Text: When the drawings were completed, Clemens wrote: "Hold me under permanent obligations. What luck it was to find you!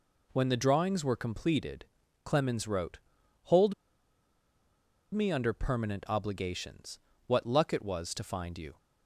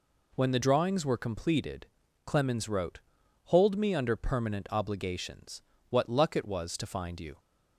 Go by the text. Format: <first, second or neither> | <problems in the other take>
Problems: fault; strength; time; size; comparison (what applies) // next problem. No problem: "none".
second | pauses between "Hold" and "me"; strong; at 3.7 s; 1.3 s long